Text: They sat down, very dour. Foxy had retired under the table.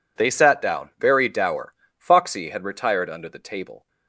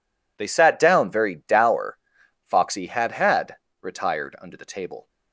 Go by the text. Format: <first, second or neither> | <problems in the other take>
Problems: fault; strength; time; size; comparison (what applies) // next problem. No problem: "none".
first | says "had" twice; at 3.1 s